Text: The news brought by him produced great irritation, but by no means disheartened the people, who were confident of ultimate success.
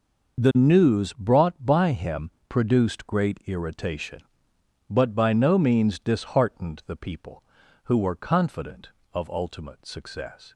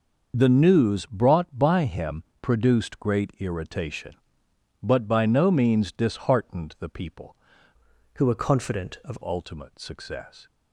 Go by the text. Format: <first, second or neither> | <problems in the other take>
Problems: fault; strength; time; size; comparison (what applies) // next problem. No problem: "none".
first | starts louder than the rest; noticeable; until 1.3 s; 6 dB // pauses between "him" and "produced"; slight; at 2.2 s; 0.16 s long; slight in the first // changes voice from "who" to "of"; from 8.1 to 9.1 s; 1.0 s long